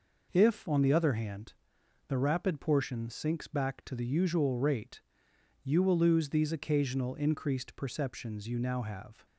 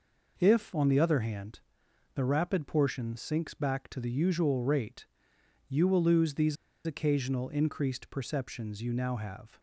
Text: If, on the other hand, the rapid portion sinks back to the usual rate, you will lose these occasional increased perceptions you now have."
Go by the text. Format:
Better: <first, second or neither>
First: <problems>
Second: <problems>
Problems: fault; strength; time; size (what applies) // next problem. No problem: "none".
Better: first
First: none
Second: pauses between "these" and "occasional"; slight; at 6.5 s; 0.29 s long